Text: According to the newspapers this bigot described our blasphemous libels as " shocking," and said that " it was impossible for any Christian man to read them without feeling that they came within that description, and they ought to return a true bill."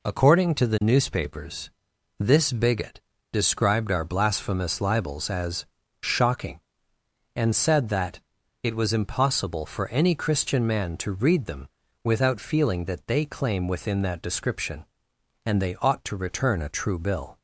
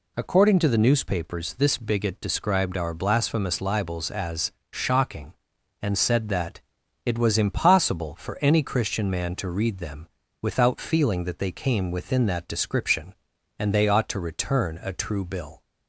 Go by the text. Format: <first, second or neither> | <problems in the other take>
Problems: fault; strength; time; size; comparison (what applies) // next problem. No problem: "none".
second | pauses between "newspapers" and "this"; noticeable; at 1.6 s; 0.50 s long // pauses between "bigot" and "described"; slight; at 2.9 s; 0.32 s long // pauses between "them" and "without"; slight; at 11.6 s; 0.34 s long; slight in the second // says "claim" for "came"; at 13.2 s